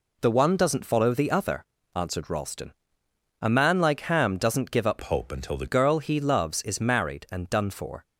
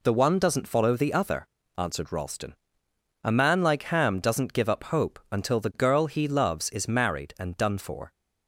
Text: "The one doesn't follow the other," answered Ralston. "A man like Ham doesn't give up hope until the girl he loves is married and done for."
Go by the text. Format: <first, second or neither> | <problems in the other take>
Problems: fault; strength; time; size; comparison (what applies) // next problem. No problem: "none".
second | changes voice from "hope" to "the"; from 5.0 to 5.6 s; 0.6 s long